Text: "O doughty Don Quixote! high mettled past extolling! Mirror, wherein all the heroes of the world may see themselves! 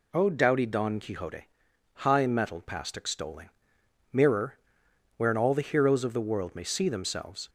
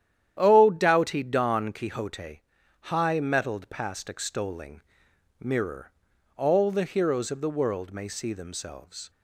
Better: first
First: none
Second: starts louder than the rest; strong; until 1.4 s; 10.5 dB // skips "wherein"; at 6.1 s

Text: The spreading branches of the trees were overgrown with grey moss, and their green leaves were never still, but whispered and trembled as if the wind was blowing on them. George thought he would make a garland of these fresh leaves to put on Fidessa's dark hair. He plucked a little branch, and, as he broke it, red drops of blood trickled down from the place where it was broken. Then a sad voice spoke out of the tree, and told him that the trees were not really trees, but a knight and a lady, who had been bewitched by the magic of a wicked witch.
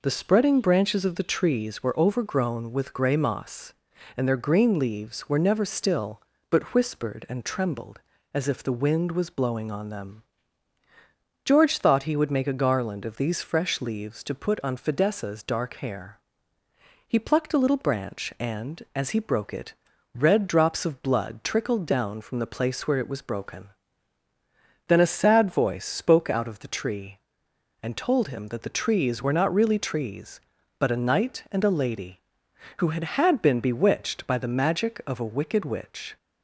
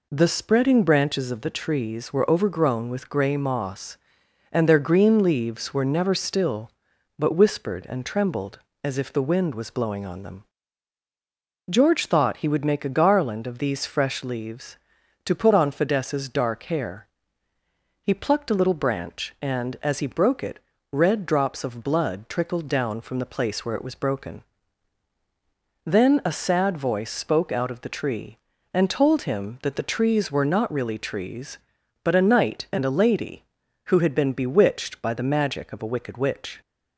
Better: second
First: says "had" twice; at 33.0 s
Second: none

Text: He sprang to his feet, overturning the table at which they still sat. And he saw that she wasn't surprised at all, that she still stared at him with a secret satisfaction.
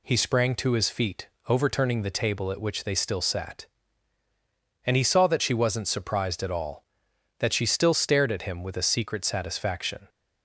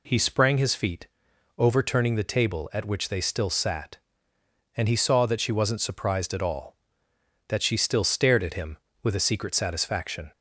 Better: first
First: none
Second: skips "to"; at 0.5 s

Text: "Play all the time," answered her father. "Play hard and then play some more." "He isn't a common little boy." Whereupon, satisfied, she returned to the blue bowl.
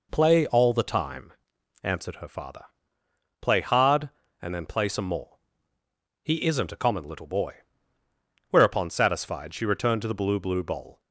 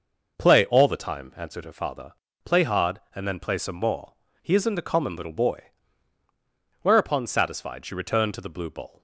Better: second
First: says "blue" twice; at 10.4 s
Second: none

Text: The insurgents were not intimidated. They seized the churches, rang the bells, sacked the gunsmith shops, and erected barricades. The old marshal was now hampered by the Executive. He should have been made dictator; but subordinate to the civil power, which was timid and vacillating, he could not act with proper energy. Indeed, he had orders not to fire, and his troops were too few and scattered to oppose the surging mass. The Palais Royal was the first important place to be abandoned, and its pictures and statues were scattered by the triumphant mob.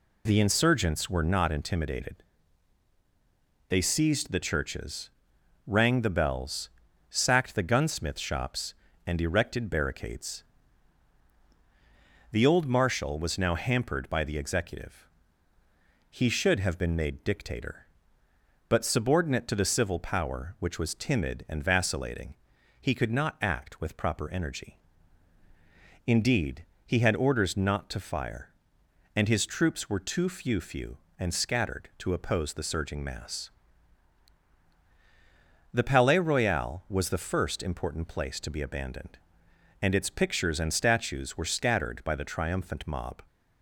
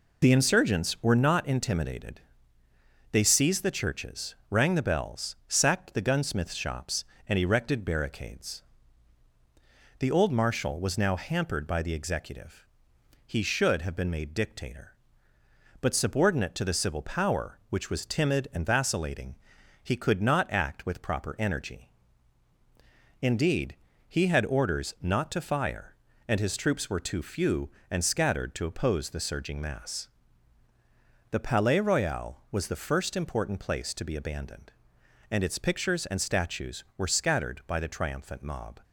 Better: second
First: says "few" twice; at 30.6 s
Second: none

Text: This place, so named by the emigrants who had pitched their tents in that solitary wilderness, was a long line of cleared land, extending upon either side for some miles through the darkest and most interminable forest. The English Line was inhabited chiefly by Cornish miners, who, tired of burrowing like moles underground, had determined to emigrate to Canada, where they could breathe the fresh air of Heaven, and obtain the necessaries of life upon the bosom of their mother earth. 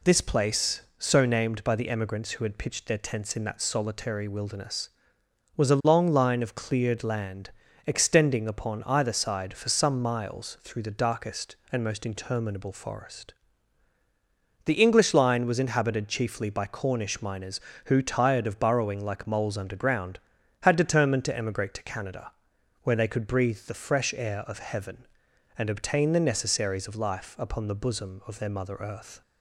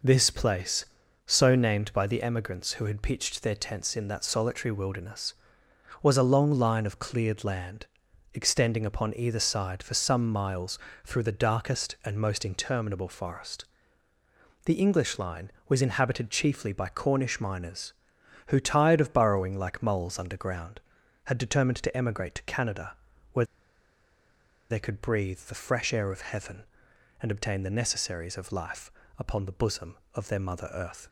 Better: first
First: none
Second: pauses between "miles" and "through"; slight; at 10.7 s; 0.24 s long // pauses between "where" and "they"; at 23.4 s; 1.2 s long // pauses between "life" and "upon"; slight; at 28.9 s; 0.26 s long

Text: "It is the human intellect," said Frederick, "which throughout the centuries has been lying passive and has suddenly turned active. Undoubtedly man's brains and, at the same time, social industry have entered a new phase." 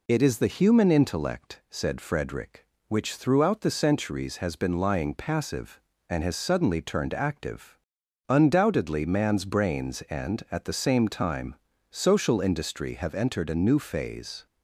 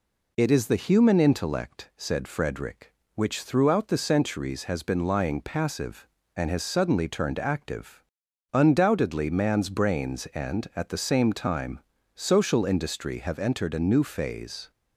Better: neither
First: none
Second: none

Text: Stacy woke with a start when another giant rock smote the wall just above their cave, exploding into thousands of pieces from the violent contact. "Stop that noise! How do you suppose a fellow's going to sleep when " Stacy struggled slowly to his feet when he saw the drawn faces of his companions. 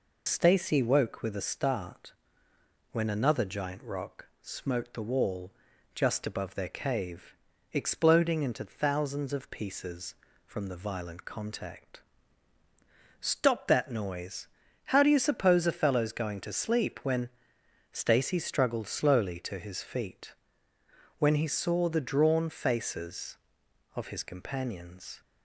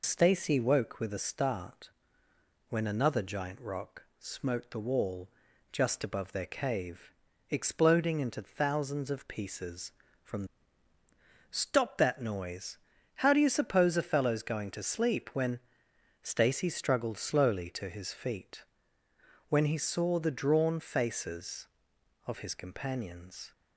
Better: first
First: pauses between "start" and "when"; noticeable; at 2.1 s; 0.80 s long // pauses between "wall" and "just"; at 5.5 s; 0.42 s long // pauses between "feet" and "when"; noticeable; at 20.3 s; 0.86 s long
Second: pauses between "start" and "when"; noticeable; at 1.8 s; 0.80 s long // pauses between "wall" and "just"; at 5.3 s; 0.42 s long // skips "the violent contact"; at 10.9 s // pauses between "feet" and "when"; noticeable; at 18.6 s; 0.86 s long

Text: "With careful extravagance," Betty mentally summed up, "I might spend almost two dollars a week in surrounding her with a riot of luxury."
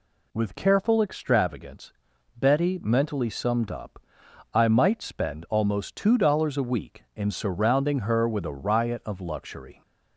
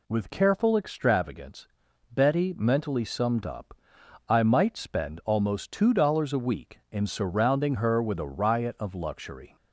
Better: neither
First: none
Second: none

